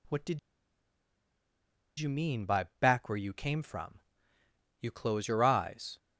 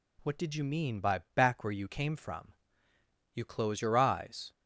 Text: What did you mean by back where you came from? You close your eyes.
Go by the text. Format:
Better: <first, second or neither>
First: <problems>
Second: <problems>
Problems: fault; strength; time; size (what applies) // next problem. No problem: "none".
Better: second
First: pauses between "did" and "you"; strong; at 0.3 s; 1.5 s long // pauses between "by" and "back"; slight; at 2.6 s; 0.16 s long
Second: pauses between "by" and "back"; slight; at 1.2 s; 0.16 s long